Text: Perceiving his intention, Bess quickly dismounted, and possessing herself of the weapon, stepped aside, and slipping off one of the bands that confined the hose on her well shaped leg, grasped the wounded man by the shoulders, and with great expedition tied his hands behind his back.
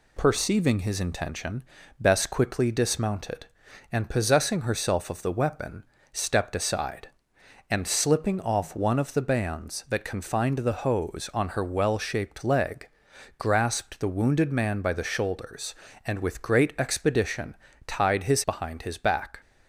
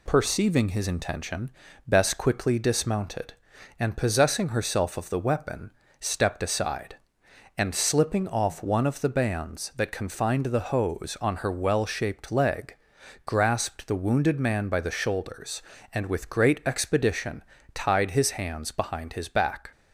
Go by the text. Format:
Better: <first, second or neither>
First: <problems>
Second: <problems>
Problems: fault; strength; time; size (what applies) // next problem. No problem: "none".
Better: second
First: pauses between "expedition" and "tied"; slight; at 17.5 s; 0.30 s long // skips "hands"; at 18.4 s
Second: pauses between "expedition" and "tied"; slight; at 17.4 s; 0.30 s long